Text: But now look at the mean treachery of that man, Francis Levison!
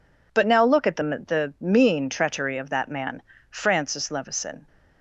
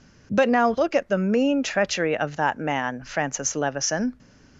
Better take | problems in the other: second | says "the" twice; at 1.0 s

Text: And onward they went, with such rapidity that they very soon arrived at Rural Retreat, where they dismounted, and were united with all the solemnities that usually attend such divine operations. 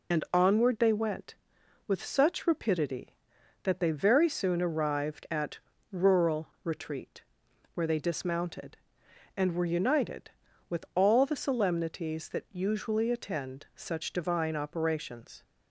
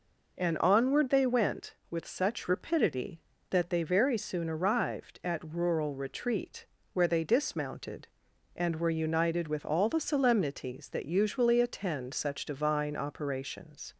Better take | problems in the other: second | loses the start of "And"; at 0.1 s; 45 ms // pauses between "at" and "Rural"; slight; at 5.5 s; 0.32 s long // pauses between "Rural" and "Retreat"; slight; at 6.4 s; 0.16 s long

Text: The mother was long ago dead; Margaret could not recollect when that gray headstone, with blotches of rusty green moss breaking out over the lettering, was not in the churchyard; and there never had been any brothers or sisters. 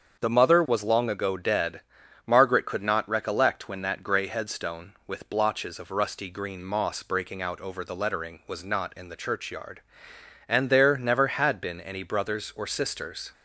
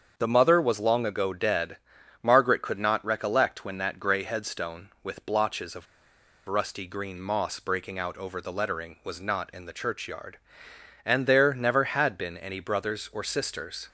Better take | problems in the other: first | starts louder than the rest; until 1.1 s; 7 dB; also in the first // pauses between "of" and "rusty"; noticeable; at 5.8 s; 0.62 s long

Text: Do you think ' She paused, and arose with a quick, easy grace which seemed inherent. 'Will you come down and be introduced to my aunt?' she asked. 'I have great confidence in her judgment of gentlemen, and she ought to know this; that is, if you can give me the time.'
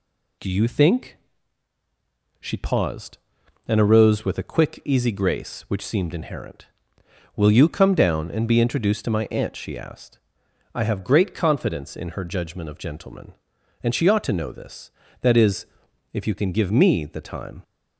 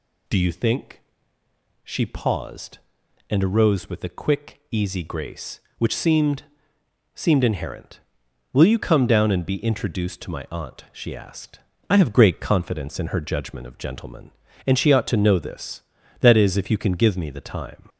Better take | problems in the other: first | says "seemed" twice; at 7.1 s

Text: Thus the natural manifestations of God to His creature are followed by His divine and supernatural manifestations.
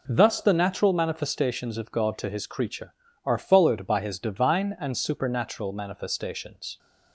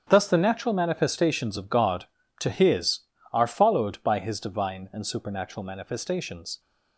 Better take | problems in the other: first | starts louder than the rest; strong; until 1.0 s; 8 dB // skips "creature"; at 3.1 s

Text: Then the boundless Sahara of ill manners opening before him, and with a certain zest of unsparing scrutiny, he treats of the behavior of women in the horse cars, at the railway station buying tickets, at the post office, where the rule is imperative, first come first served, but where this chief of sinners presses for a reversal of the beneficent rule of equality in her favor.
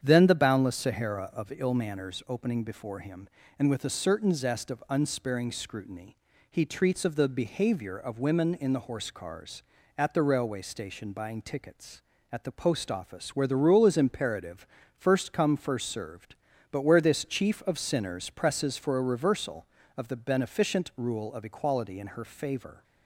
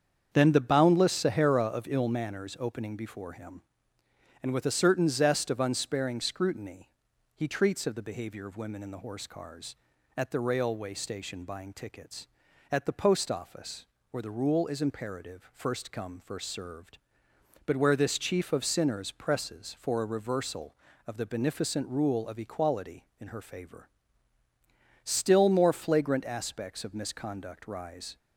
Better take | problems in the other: first | starts louder than the rest; strong; until 1.3 s; 7.5 dB; strong in the first // goes on to say "Still more flagrant aspects of misconduct rise"; strong; from 25.0 s on; 3.1 s long

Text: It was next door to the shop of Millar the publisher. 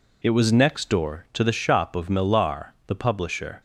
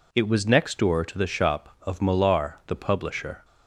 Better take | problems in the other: neither | none

